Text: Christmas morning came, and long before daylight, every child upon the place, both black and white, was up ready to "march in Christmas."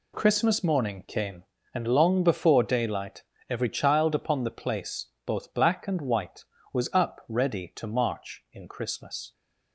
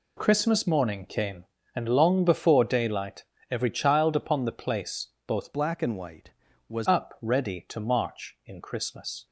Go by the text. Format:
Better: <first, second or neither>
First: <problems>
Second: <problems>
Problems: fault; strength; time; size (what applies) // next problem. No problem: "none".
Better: first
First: none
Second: changes voice from "black" to "was"; from 5.5 to 6.8 s; 1.3 s long